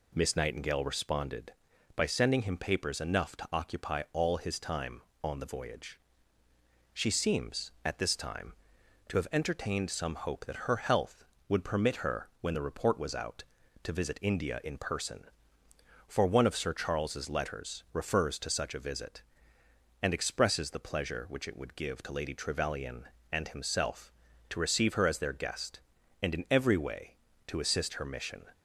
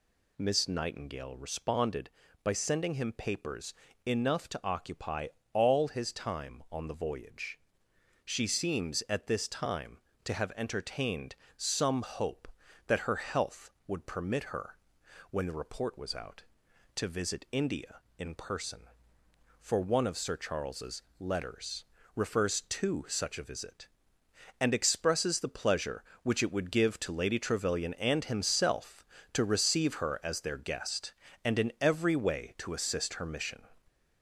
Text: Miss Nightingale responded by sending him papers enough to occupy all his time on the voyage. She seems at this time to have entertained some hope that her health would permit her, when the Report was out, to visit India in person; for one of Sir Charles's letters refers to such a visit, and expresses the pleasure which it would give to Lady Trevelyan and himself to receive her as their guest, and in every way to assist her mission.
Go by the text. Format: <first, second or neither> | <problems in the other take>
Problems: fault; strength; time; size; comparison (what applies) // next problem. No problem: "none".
first | gets louder; slight; throughout; 3 dB // pauses between "papers" and "enough"; slight; at 3.7 s; 0.32 s long // pauses between "occupy" and "all"; slight; at 5.2 s; 0.26 s long // pauses between "entertained" and "some"; slight; at 11.3 s; 0.22 s long // pauses between "Charles's" and "letters"; slight; at 21.0 s; 0.18 s long // pauses between "letters" and "refers"; slight; at 21.8 s; 0.30 s long